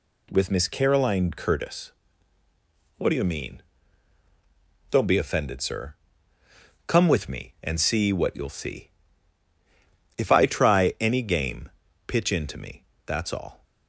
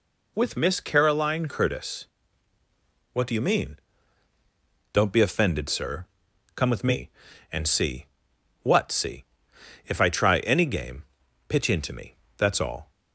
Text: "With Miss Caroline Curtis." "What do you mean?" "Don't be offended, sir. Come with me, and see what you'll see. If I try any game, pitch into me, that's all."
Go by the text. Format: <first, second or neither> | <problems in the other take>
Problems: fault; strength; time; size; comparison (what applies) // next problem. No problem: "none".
first | pauses between "see" and "what"; noticeable; at 8.0 s; 0.58 s long // skips "you'll"; at 8.8 s